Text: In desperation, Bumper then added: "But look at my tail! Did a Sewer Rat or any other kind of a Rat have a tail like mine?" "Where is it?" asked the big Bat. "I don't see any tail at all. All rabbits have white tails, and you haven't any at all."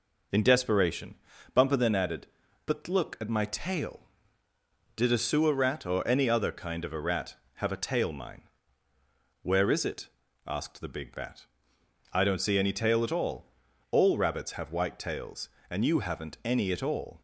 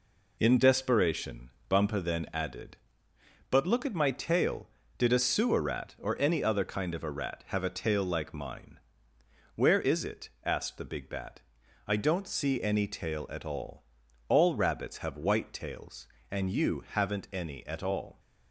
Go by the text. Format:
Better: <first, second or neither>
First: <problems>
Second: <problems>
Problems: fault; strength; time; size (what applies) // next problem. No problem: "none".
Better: second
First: skips "like"; at 8.1 s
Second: none